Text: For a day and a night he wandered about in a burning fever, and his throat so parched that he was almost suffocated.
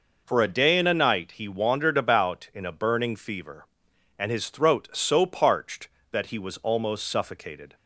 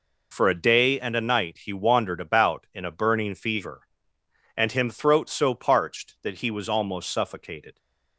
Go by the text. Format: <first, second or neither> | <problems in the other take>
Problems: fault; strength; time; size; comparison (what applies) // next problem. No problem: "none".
first | says "him" for "his"; at 4.7 s